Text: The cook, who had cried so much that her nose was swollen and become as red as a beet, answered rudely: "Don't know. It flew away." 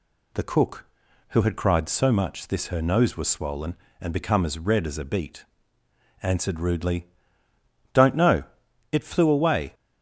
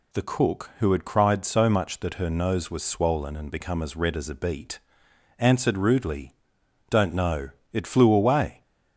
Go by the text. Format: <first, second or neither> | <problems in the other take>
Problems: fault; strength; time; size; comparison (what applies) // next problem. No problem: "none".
second | says "this" for "that"; at 2.4 s